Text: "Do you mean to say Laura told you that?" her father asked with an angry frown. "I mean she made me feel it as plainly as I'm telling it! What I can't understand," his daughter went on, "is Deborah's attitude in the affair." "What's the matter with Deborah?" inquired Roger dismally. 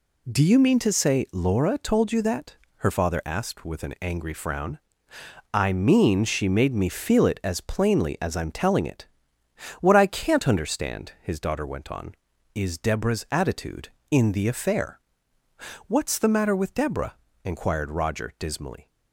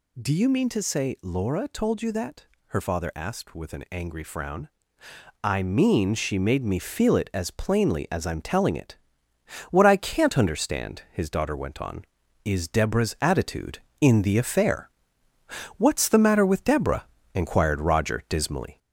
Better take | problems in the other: first | gets louder; slight; throughout; 3 dB

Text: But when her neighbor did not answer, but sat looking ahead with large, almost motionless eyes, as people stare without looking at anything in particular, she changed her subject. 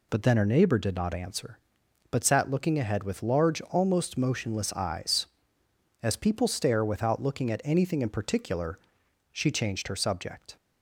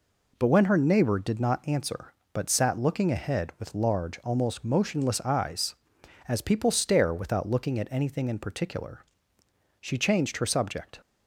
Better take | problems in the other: second | says "then" for "when"; at 0.2 s

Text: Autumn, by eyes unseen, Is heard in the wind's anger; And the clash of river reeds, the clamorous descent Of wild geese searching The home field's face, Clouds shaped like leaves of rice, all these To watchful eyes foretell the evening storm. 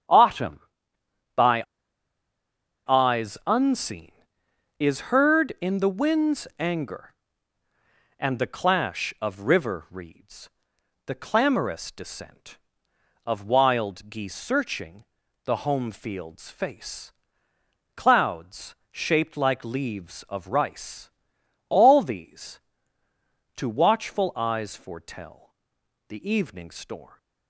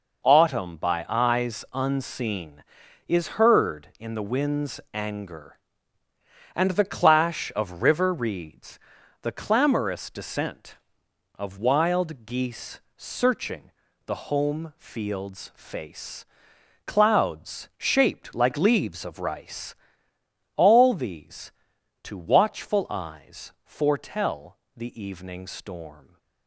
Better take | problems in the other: second | starts louder than the rest; strong; until 3.0 s; 9.5 dB // pauses between "by" and "eyes"; at 1.6 s; 1.2 s long // pauses between "searching" and "The"; at 15.0 s; 0.40 s long; slight in the second // pauses between "Clouds" and "shaped"; slight; at 18.7 s; 0.20 s long // pauses between "foretell" and "the"; noticeable; at 25.5 s; 0.54 s long; slight in the second

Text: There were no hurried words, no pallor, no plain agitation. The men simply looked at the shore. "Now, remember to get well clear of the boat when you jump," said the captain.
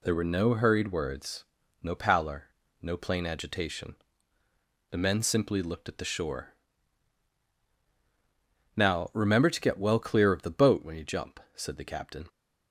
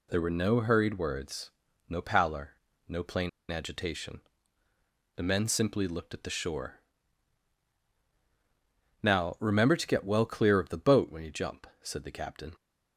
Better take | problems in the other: first | pauses between "plain" and "agitation"; slight; at 3.2 s; 0.20 s long

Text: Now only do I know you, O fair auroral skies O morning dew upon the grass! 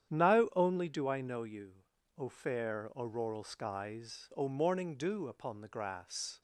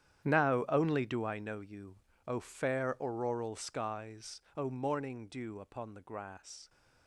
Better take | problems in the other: first | gets quieter; strong; throughout; 15.5 dB // starts louder than the rest; strong; until 1.3 s; 10 dB; strong in the first // pauses between "skies" and "O"; slight; at 4.3 s; 0.16 s long

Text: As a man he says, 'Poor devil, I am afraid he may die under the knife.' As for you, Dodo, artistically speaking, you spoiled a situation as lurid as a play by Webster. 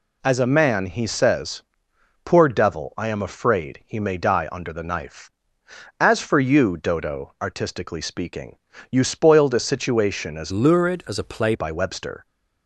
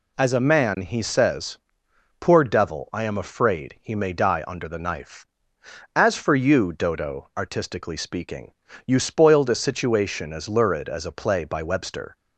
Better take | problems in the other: second | changes voice from "lurid" to "play"; from 10.5 to 11.5 s; 1.0 s long

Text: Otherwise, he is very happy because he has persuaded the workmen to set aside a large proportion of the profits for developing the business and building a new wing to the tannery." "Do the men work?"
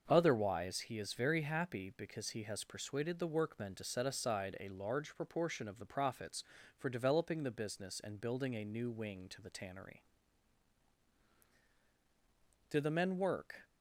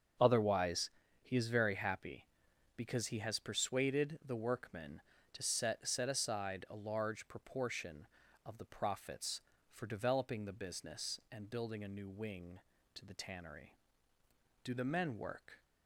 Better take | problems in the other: first | starts louder than the rest; until 1.5 s; 6.5 dB; also in the first // says "set" twice; at 5.8 s

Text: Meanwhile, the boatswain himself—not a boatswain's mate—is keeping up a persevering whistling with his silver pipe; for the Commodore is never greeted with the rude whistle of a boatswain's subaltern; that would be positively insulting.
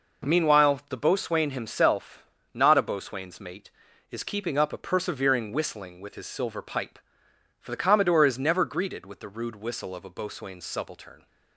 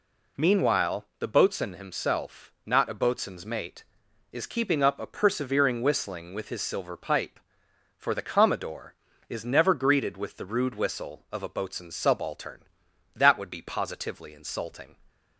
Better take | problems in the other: second | stops before "that would be positively insulting"; at 11.2 s

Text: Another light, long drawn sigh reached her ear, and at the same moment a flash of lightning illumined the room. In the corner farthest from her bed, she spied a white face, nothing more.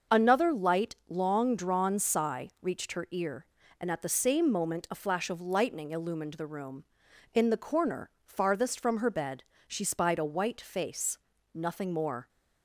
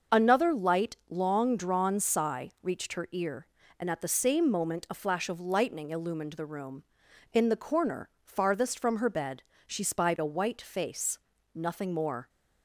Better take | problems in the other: neither | starts louder than the rest; the same in both

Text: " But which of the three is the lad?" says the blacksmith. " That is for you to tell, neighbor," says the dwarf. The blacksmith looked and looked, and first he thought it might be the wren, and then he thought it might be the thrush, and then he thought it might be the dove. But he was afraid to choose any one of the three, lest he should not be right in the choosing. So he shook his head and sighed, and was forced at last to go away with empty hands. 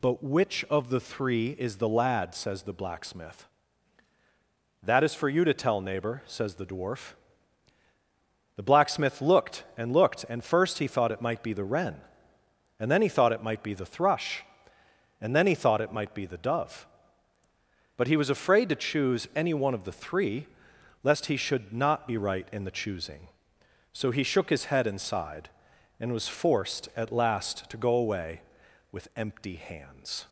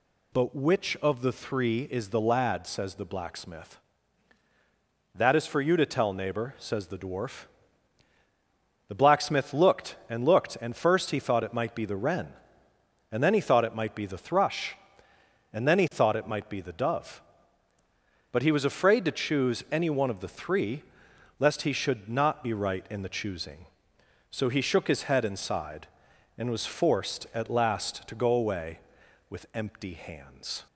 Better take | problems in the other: neither | none

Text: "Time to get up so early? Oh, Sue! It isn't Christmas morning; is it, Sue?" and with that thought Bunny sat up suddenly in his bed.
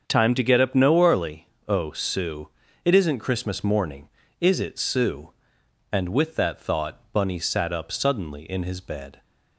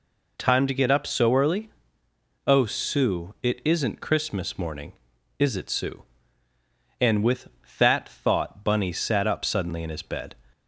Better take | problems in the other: second | starts louder than the rest; strong; until 1.0 s; 7 dB // says "no" for "so"; at 0.7 s

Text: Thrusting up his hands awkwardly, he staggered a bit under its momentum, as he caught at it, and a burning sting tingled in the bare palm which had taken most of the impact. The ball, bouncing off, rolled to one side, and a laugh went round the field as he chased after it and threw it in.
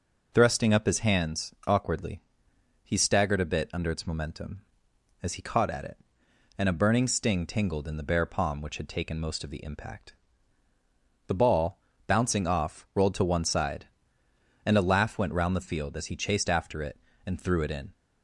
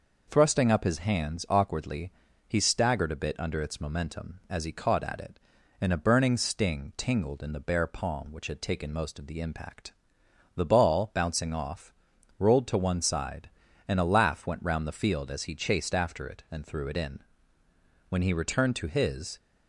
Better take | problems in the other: first | goes on to say "When he returned to his"; noticeable; from 18.0 s on; 1.3 s long

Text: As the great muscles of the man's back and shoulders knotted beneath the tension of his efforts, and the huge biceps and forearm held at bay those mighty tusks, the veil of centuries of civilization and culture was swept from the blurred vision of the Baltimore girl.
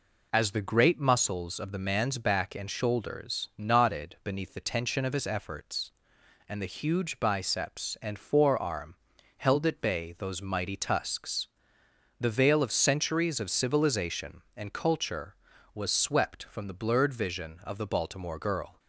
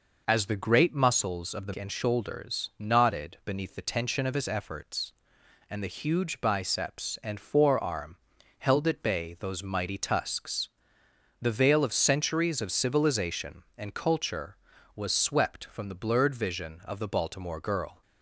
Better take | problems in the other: first | skips "man's back"; at 1.7 s // pauses between "forearm" and "held"; at 8.1 s; 0.44 s long; also in the first

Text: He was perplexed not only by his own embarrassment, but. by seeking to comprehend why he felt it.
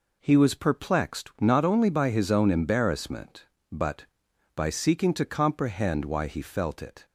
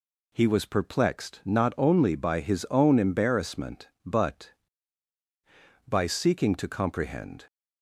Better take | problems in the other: first | stops before "why he felt it"; at 7.4 s

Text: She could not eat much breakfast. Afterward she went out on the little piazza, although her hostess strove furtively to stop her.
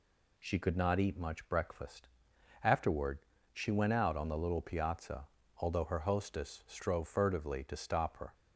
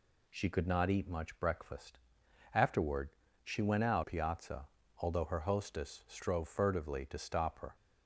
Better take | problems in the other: first | pauses between "Afterward" and "she"; slight; at 3.0 s; 0.36 s long; slight in the first // skips "on the little"; at 4.0 s

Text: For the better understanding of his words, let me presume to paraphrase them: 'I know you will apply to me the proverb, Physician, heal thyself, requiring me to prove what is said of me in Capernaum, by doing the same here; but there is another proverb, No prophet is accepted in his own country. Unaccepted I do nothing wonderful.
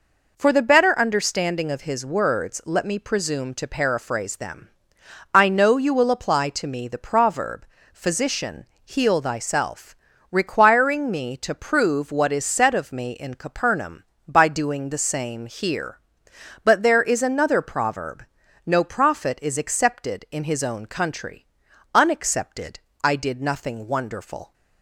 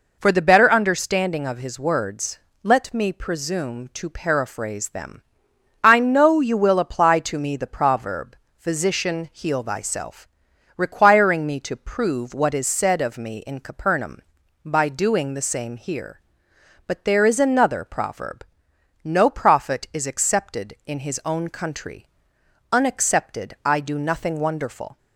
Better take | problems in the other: second | pauses between "Unaccepted" and "I"; slight; at 22.8 s; 0.24 s long // says "did" for "do"; at 23.1 s

